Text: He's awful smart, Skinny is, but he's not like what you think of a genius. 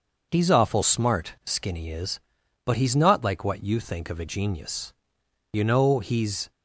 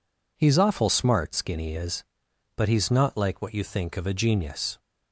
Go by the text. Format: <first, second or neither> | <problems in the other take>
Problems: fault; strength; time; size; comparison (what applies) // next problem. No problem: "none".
second | goes on to say "You know he's"; noticeable; from 5.5 s on; 0.98 s long